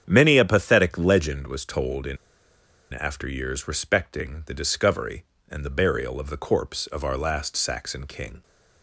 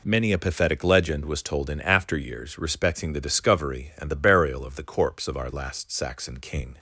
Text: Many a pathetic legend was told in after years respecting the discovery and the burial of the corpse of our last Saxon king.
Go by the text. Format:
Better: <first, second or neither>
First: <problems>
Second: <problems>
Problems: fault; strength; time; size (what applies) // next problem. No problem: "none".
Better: second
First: starts louder than the rest; strong; until 1.0 s; 8.5 dB // pauses between "in" and "after"; noticeable; at 2.1 s; 0.75 s long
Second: none